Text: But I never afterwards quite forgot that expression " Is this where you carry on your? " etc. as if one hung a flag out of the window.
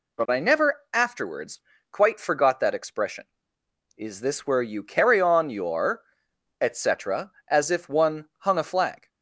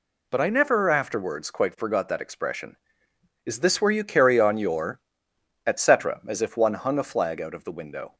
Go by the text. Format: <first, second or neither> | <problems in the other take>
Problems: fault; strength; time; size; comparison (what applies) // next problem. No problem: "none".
second | pauses between "afterwards" and "quite"; slight; at 1.6 s; 0.30 s long // stops before "out of the window"; at 9.0 s